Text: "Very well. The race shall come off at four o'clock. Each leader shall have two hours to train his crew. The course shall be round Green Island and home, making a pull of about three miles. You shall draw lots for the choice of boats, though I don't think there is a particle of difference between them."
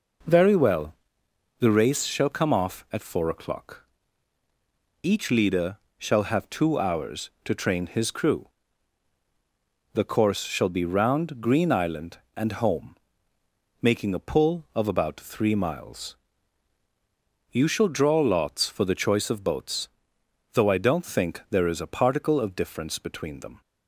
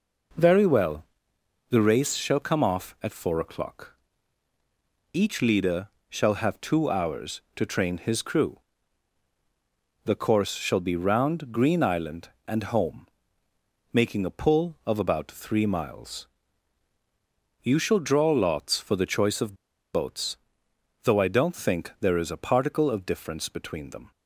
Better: first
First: pauses between "leader" and "shall"; slight; at 5.7 s; 0.18 s long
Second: pauses between "leader" and "shall"; slight; at 5.8 s; 0.18 s long // pauses between "of" and "boats"; at 19.5 s; 0.37 s long

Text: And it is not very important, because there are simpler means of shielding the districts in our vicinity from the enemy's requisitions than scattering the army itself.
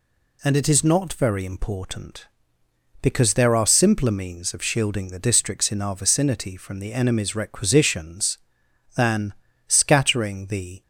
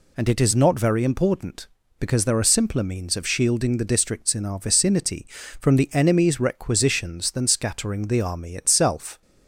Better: second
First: pauses between "than" and "scattering"; slight; at 9.3 s; 0.34 s long // stops before "army itself"; at 10.8 s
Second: none

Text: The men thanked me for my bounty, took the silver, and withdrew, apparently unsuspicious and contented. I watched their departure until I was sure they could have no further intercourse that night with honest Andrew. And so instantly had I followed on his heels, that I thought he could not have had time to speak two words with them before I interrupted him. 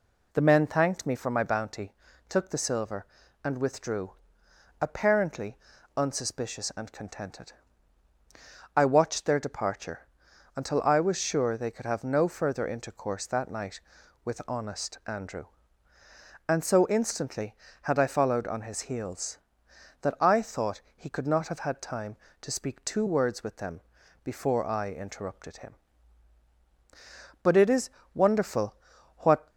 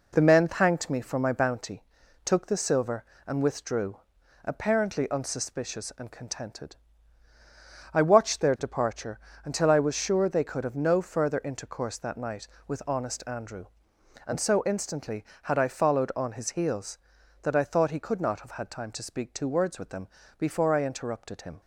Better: second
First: pauses between "apparently" and "unsuspicious"; at 5.5 s; 0.40 s long // pauses between "departure" and "until"; noticeable; at 10.0 s; 0.48 s long // pauses between "them" and "before"; at 23.8 s; 0.42 s long // goes on to say "But it is wonderful what"; strong; from 27.4 s on; 2.0 s long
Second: pauses between "departure" and "until"; slight; at 9.1 s; 0.26 s long // pauses between "them" and "before"; slight; at 20.0 s; 0.30 s long

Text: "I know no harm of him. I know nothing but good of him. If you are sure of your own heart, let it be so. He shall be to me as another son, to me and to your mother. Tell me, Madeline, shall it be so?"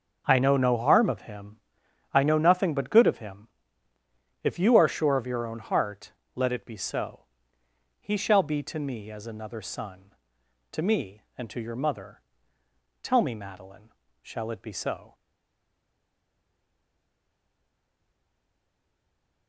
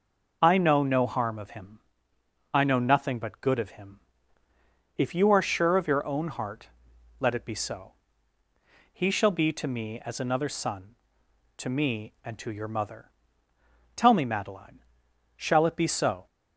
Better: second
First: stays silent after the last word; strong; from 15.1 s on; 4.3 s long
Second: none

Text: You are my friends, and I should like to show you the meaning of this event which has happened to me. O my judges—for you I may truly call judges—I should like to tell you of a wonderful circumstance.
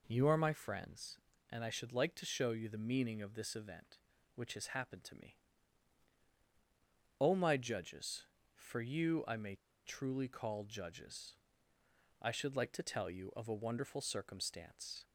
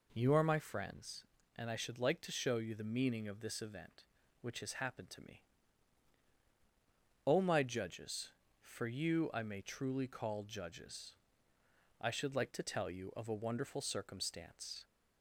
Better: second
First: pauses between "may" and "truly"; slight; at 9.5 s; 0.29 s long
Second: none

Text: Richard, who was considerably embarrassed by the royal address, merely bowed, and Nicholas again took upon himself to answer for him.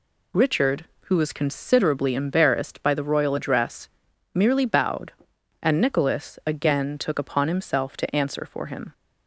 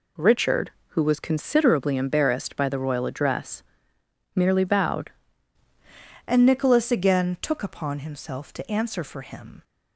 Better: first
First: none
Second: changes voice at "and"; from 6.2 s on; 3.4 s long

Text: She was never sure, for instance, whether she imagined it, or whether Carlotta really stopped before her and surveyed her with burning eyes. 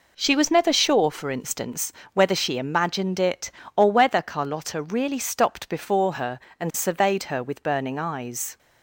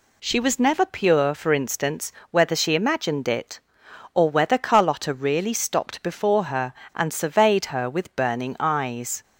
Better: first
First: none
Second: says "pure" for "sure"; at 0.8 s

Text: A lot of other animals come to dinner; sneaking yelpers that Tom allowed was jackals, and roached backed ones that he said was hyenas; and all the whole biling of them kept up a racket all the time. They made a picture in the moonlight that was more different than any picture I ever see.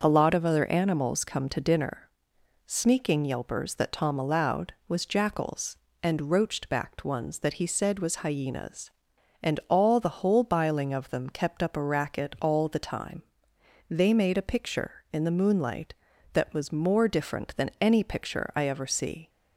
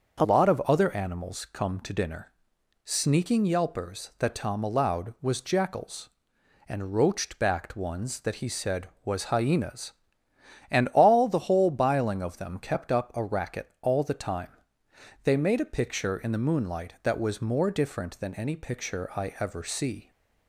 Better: first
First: starts louder than the rest; noticeable; until 1.0 s; 6 dB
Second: starts louder than the rest; until 1.2 s; 6.5 dB // changes voice at "lot"; from 0.2 s on; 19.8 s long

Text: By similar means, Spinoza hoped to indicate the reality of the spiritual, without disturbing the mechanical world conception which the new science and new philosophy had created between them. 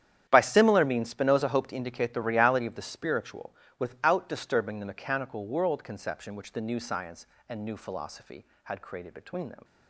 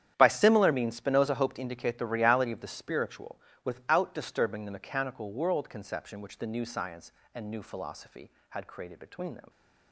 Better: neither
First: starts louder than the rest; strong; until 1.2 s; 10 dB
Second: starts louder than the rest; strong; until 1.1 s; 10 dB

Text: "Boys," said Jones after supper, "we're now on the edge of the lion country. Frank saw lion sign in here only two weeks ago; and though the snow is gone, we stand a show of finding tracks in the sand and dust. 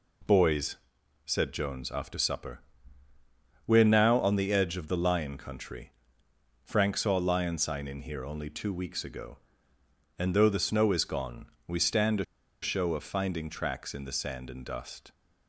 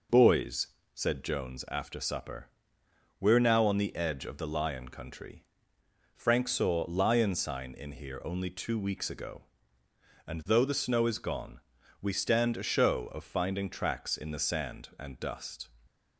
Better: second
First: pauses between "a" and "show"; at 12.2 s; 0.37 s long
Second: none

